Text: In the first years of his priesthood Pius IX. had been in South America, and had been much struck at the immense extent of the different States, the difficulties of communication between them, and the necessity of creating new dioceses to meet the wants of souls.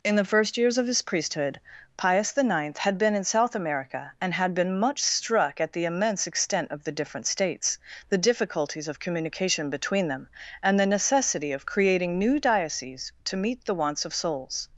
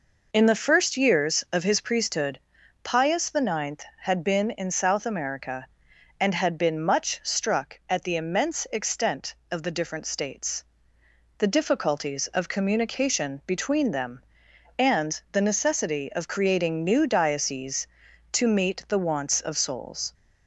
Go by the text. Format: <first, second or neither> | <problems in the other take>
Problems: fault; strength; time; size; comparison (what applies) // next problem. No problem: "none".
neither | pauses between "priesthood" and "Pius"; the same in both